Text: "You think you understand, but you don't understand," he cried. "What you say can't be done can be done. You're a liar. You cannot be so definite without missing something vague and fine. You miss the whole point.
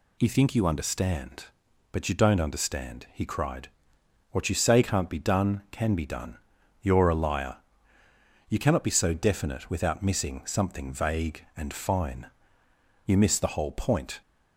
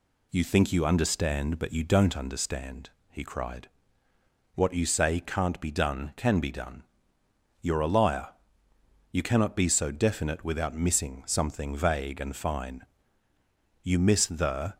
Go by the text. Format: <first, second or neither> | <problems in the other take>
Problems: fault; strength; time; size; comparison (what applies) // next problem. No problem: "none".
first | stops before "whole point"; at 14.7 s